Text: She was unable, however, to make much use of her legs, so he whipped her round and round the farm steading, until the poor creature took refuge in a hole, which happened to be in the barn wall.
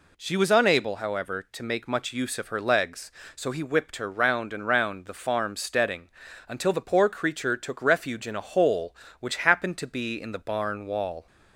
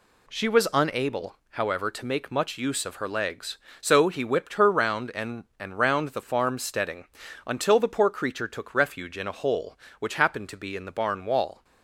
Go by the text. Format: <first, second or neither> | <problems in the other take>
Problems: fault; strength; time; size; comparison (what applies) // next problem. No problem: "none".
first | says "and" twice; at 5.5 s